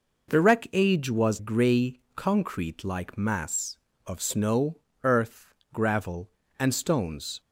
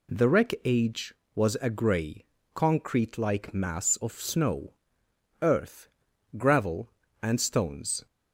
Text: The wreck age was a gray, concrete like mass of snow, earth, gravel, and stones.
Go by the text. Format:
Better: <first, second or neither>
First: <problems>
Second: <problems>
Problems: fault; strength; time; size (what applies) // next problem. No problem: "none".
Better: second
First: skips "a"; at 1.3 s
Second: none